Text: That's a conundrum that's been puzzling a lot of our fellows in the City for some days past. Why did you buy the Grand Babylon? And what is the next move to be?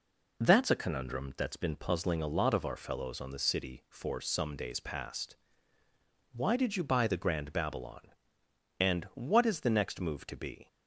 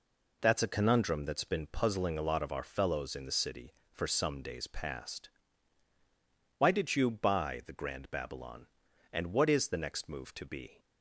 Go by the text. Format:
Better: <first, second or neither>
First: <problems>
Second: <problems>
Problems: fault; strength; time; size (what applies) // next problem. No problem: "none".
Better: second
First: says "on" for "in"; at 3.2 s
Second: none